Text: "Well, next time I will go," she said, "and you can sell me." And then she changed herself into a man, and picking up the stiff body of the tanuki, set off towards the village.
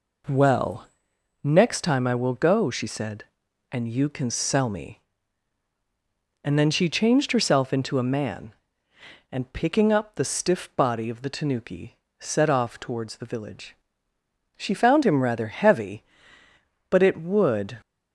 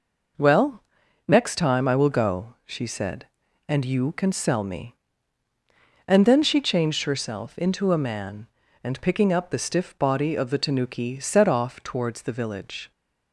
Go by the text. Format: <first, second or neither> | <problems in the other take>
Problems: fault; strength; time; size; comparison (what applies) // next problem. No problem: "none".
second | goes on to say "She found him rather heavy but it would"; strong; from 14.5 s on; 3.2 s long